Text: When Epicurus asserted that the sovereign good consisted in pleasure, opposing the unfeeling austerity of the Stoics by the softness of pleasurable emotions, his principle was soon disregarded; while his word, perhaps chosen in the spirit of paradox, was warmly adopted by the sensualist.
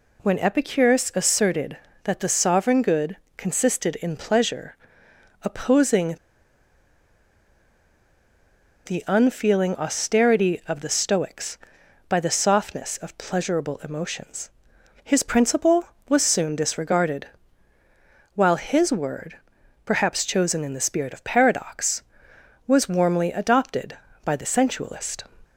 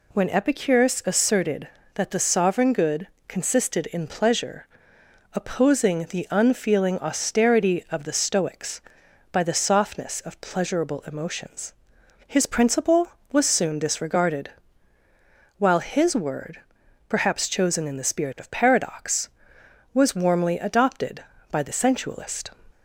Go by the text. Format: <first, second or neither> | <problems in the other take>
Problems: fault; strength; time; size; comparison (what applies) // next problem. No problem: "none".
second | pauses between "good" and "consisted"; slight; at 3.1 s; 0.22 s long; slight in the second // pauses between "opposing" and "the"; strong; at 6.1 s; 2.7 s long